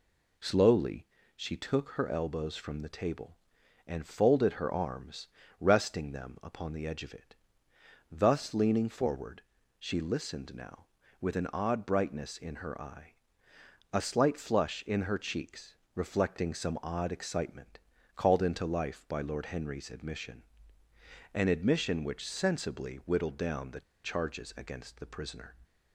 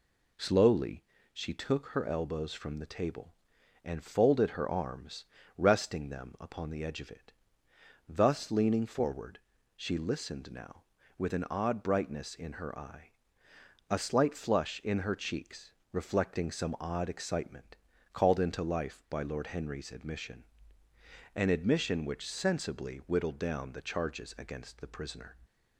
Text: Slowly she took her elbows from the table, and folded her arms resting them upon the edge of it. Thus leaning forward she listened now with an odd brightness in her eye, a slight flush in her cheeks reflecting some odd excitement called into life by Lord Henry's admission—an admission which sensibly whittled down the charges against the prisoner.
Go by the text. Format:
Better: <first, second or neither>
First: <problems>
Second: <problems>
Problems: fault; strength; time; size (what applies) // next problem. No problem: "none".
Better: second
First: pauses between "Slowly" and "she"; slight; at 1.0 s; 0.30 s long // pauses between "arms" and "resting"; slight; at 5.2 s; 0.32 s long // pauses between "forward" and "she"; at 9.4 s; 0.38 s long // pauses between "cheeks" and "reflecting"; slight; at 15.7 s; 0.22 s long // pauses between "excitement" and "called"; slight; at 17.7 s; 0.36 s long // pauses between "the" and "charges"; slight; at 23.8 s; 0.23 s long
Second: pauses between "Slowly" and "she"; slight; at 1.0 s; 0.30 s long // pauses between "arms" and "resting"; slight; at 5.2 s; 0.32 s long // pauses between "forward" and "she"; at 9.3 s; 0.38 s long // pauses between "cheeks" and "reflecting"; slight; at 15.7 s; 0.22 s long // pauses between "excitement" and "called"; slight; at 17.7 s; 0.36 s long